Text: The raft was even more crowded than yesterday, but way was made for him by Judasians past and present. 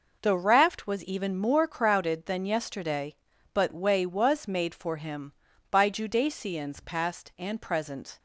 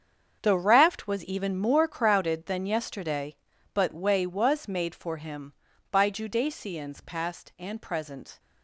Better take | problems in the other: first | gets quieter; strong; throughout; 13 dB

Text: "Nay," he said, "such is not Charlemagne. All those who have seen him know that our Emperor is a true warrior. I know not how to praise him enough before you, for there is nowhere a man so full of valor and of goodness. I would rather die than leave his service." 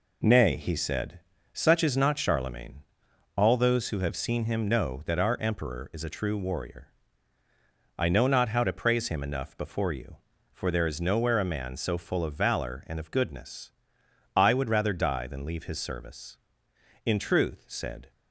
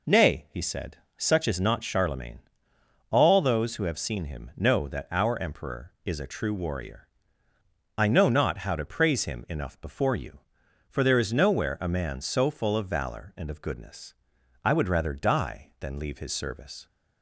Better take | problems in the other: second | goes on to say "In truth said"; noticeable; from 17.0 s on; 1.0 s long

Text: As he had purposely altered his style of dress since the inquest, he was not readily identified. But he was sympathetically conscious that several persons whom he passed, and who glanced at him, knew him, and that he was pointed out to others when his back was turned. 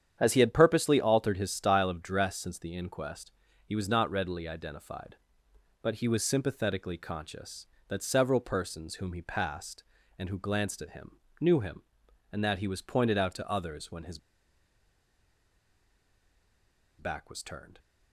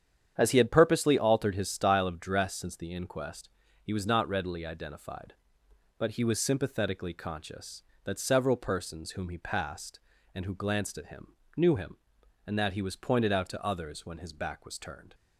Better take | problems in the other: second | starts louder than the rest; strong; until 1.2 s; 9 dB; strong in the second // pauses between "his" and "back"; strong; at 14.1 s; 2.8 s long

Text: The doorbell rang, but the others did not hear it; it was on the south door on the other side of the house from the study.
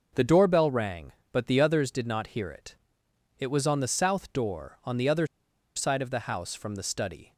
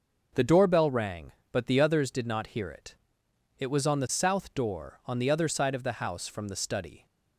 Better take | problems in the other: second | pauses between "other" and "side"; noticeable; at 5.2 s; 0.50 s long

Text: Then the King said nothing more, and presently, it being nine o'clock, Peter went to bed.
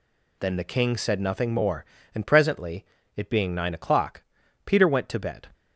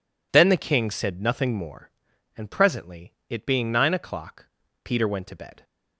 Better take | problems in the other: neither | none

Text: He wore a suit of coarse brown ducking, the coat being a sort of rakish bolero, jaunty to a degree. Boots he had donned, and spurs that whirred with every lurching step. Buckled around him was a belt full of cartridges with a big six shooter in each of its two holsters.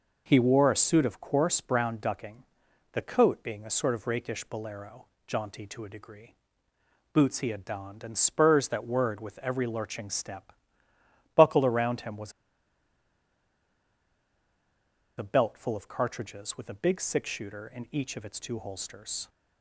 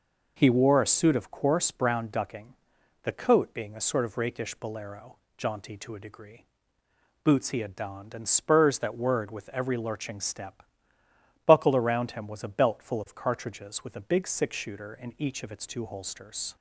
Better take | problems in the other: second | pauses between "was" and "a"; strong; at 12.3 s; 2.8 s long

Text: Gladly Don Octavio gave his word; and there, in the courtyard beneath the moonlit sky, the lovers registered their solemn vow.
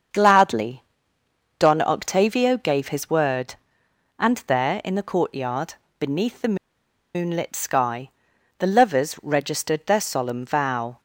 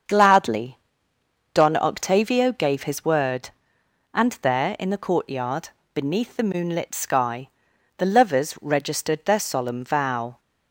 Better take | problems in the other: second | starts louder than the rest; until 1.8 s; 7 dB; also in the second // pauses between "Gladly" and "Don"; noticeable; at 0.8 s; 0.74 s long; noticeable in the second // pauses between "courtyard" and "beneath"; slight; at 5.7 s; 0.26 s long; slight in the second // pauses between "the" and "moonlit"; noticeable; at 6.5 s; 0.59 s long

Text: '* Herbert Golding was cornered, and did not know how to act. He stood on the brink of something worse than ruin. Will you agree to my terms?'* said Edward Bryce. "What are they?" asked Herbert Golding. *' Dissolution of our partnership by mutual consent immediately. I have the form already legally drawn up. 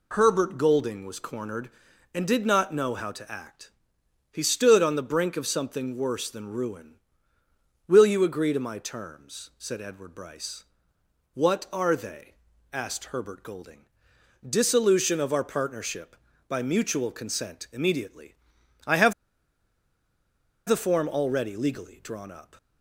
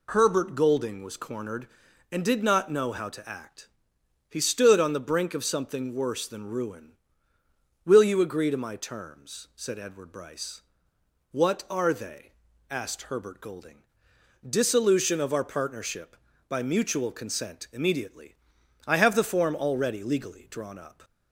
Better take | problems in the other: second | pauses between "have" and "the"; strong; at 19.1 s; 1.5 s long

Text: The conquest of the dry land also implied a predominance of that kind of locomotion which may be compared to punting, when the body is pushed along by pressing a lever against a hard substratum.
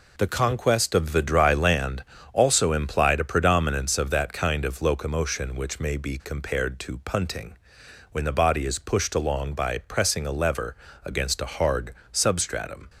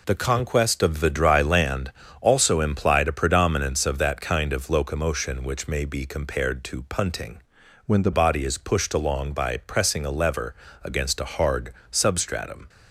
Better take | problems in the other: first | pauses between "land" and "also"; slight; at 1.9 s; 0.28 s long; slight in the first // changes voice from "when" to "the"; from 7.8 to 8.1 s; 0.3 s long // pauses between "lever" and "against"; slight; at 10.5 s; 0.30 s long; slight in the first // pauses between "hard" and "substratum"; slight; at 11.7 s; 0.18 s long; slight in the first

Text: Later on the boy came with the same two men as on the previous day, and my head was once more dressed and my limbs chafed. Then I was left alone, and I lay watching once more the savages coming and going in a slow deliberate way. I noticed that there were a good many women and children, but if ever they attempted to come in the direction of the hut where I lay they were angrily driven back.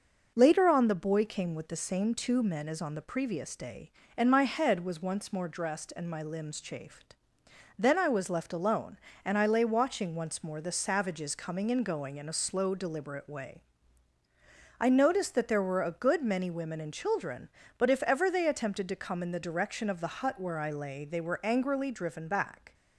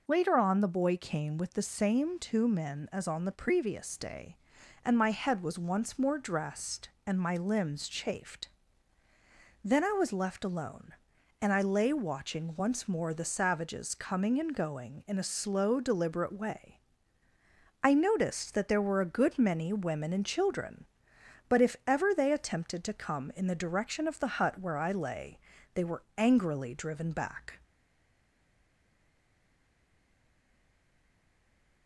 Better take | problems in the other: first | pauses between "lay" and "they"; slight; at 25.3 s; 0.34 s long // stays silent after the last word; strong; from 27.6 s on; 4.2 s long

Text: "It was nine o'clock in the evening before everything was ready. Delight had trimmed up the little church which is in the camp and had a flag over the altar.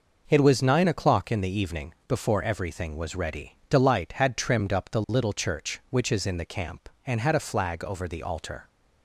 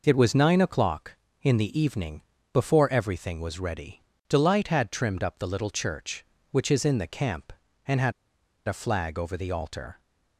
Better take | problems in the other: first | pauses between "evening" and "before"; slight; at 2.2 s; 0.32 s long // pauses between "had" and "a"; noticeable; at 8.1 s; 0.53 s long

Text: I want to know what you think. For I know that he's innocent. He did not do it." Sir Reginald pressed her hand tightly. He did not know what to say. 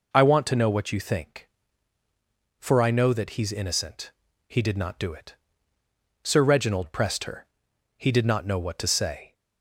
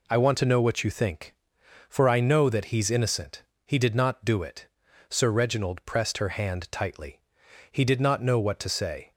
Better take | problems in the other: second | skips "hand tightly"; at 7.7 s

